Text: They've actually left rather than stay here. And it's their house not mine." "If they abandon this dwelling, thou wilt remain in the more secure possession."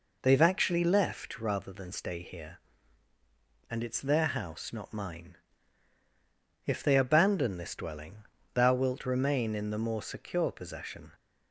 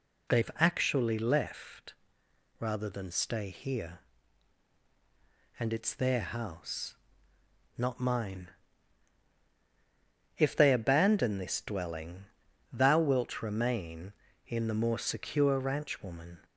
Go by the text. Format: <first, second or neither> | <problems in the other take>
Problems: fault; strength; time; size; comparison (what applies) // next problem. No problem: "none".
first | pauses between "left" and "rather"; noticeable; at 1.9 s; 0.66 s long // pauses between "house" and "not"; noticeable; at 6.9 s; 0.82 s long // says "ranchwoman" for "possession"; at 15.5 s